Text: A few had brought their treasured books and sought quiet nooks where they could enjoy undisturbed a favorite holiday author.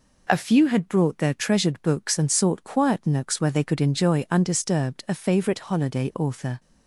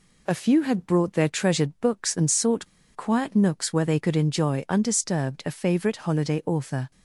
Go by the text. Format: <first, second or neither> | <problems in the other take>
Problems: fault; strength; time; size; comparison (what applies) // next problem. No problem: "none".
first | pauses between "sought" and "quiet"; slight; at 2.6 s; 0.28 s long